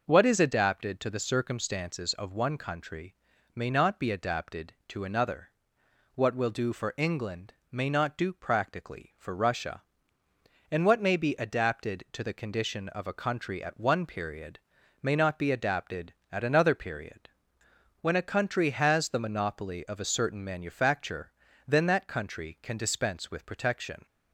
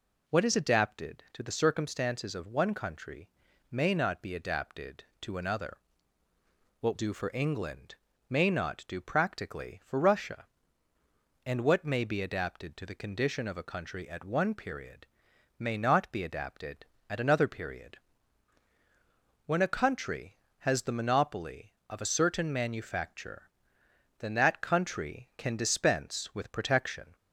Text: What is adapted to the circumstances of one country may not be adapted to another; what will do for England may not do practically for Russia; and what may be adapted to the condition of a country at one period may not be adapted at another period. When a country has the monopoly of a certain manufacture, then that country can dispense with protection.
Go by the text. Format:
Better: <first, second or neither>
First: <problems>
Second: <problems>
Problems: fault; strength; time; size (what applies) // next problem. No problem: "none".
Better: first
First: pauses between "country" and "may"; at 3.1 s; 0.40 s long // pauses between "England" and "may"; slight; at 7.5 s; 0.18 s long // pauses between "period" and "may"; at 14.5 s; 0.42 s long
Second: pauses between "country" and "may"; at 3.2 s; 0.42 s long // skips "will"; at 6.9 s // pauses between "England" and "may"; slight; at 7.9 s; 0.34 s long // pauses between "period" and "may"; noticeable; at 15.0 s; 0.50 s long